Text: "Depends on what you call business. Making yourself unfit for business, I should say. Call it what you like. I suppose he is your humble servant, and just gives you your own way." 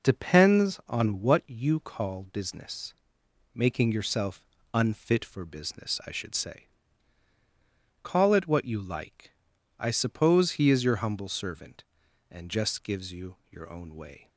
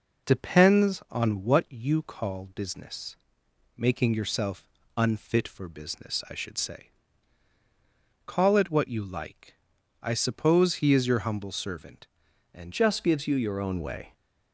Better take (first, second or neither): first